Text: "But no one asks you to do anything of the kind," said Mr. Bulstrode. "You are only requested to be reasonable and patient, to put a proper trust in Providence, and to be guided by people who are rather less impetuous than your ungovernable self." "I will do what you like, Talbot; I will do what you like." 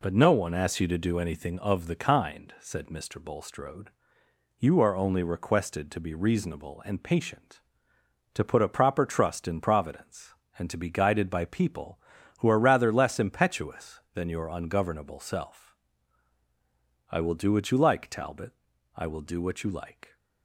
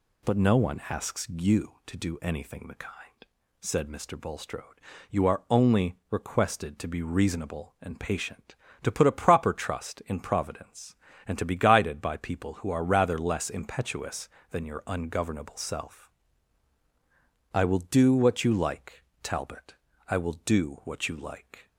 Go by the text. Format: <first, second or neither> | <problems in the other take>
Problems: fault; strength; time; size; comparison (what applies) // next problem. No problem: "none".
first | skips "of"; at 2.6 s